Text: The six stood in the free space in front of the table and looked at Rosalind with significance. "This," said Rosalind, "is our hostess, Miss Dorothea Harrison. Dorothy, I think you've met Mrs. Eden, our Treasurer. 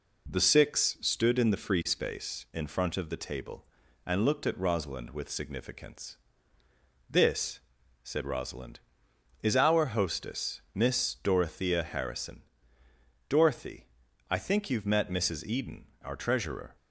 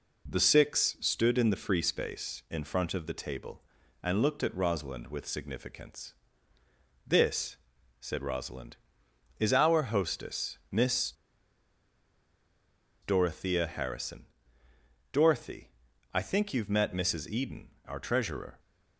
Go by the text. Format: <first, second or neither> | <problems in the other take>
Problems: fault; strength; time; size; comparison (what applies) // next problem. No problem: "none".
first | pauses between "Miss" and "Dorothea"; strong; at 11.1 s; 1.8 s long